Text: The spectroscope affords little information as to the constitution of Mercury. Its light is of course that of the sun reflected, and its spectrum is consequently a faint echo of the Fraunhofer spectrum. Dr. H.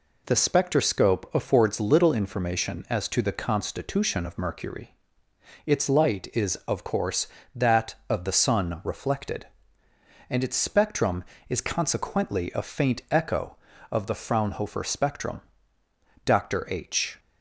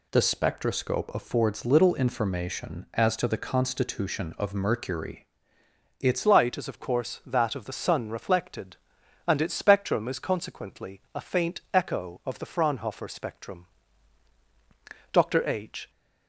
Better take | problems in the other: first | changes voice at "light"; from 6.2 s on; 9.6 s long

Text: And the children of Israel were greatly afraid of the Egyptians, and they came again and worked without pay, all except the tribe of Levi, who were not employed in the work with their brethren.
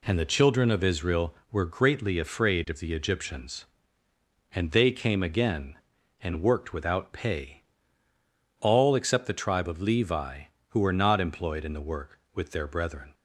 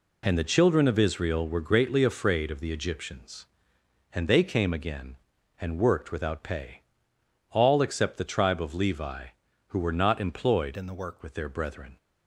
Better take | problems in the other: first | changes voice from "in" to "work"; from 10.7 to 11.2 s; 0.5 s long

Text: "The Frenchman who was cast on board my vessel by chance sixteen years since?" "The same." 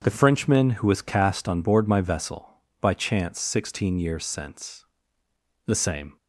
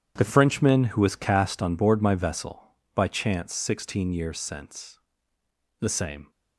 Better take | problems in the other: first | gets quieter; strong; throughout; 14 dB // starts louder than the rest; strong; until 1.1 s; 9.5 dB; strong in the first

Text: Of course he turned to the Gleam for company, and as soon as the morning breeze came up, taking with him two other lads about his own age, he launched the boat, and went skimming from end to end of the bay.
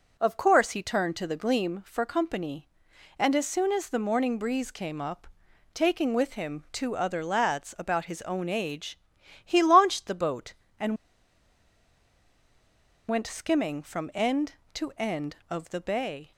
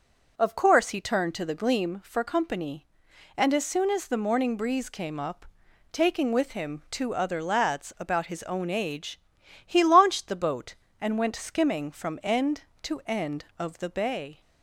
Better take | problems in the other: second | pauses between "and" and "went"; strong; at 10.9 s; 2.1 s long

